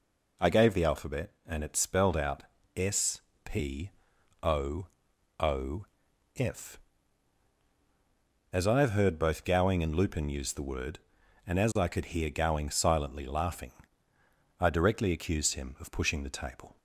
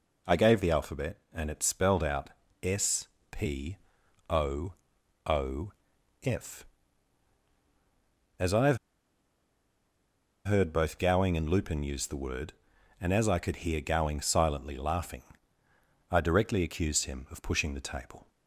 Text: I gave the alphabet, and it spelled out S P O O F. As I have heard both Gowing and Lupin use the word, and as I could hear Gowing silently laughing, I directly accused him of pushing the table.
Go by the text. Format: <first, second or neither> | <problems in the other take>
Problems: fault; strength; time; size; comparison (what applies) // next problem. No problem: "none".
first | pauses between "out" and "S"; slight; at 2.2 s; 0.32 s long; slight in the first // pauses between "S" and "P"; slight; at 3.0 s; 0.24 s long; slight in the first // pauses between "P" and "O"; noticeable; at 3.7 s; 0.52 s long; noticeable in the first // pauses between "O" and "O"; noticeable; at 4.7 s; 0.52 s long; noticeable in the first // pauses between "O" and "F"; noticeable; at 5.7 s; 0.52 s long; noticeable in the first // pauses between "have" and "heard"; strong; at 8.7 s; 1.6 s long